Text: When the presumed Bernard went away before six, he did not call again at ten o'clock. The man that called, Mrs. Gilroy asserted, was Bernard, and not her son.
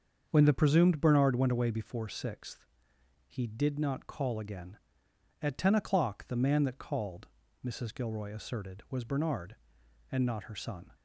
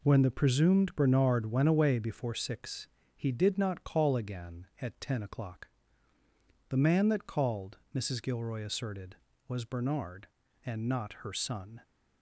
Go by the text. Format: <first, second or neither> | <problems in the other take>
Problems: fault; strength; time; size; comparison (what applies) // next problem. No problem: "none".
second | starts louder than the rest; until 1.3 s; 7 dB // says "sixth" for "six"; at 2.0 s